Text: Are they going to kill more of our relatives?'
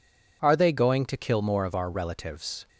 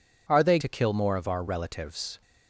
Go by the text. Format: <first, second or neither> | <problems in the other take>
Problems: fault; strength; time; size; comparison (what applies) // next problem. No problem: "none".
first | skips "going"; at 0.5 s